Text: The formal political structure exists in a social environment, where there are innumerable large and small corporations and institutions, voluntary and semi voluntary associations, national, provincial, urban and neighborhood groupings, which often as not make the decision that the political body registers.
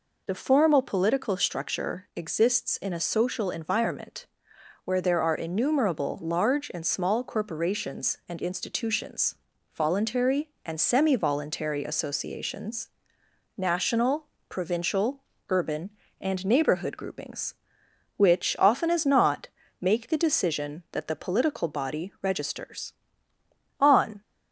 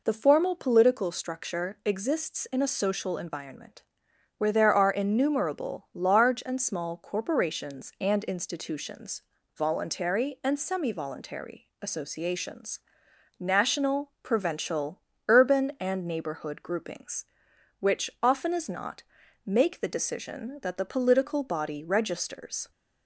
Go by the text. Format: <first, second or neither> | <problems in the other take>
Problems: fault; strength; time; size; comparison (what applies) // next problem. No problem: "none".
second | pauses between "not" and "make"; slight; at 19.4 s; 0.34 s long; also in the second // goes on to say "On"; slight; from 23.8 s on; 0.40 s long